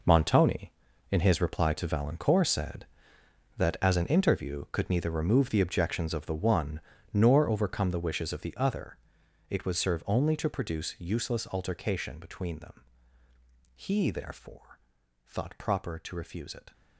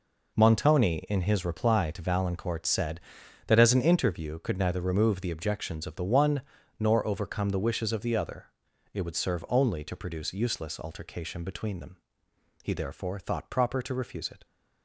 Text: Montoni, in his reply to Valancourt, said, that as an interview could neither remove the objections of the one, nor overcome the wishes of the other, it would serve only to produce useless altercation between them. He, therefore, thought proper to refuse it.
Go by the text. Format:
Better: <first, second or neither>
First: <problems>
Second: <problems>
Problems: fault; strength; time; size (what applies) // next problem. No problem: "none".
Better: second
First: gets quieter; strong; throughout; 12.5 dB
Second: none